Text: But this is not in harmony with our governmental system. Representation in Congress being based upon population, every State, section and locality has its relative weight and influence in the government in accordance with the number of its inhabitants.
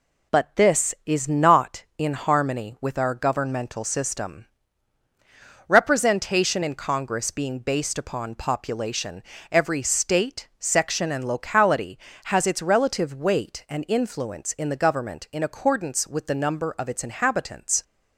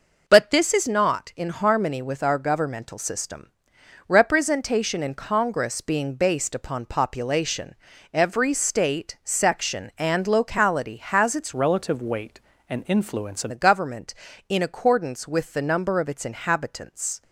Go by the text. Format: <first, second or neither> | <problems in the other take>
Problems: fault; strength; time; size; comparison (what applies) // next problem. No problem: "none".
first | changes voice from "relative" to "in"; from 11.5 to 13.5 s; 2.0 s long